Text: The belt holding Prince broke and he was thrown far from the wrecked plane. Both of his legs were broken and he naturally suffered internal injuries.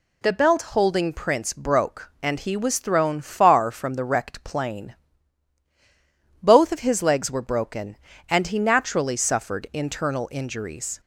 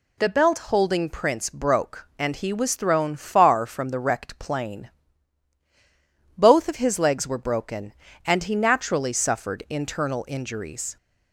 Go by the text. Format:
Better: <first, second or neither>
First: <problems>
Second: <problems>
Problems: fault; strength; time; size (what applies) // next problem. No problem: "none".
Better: neither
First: none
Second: none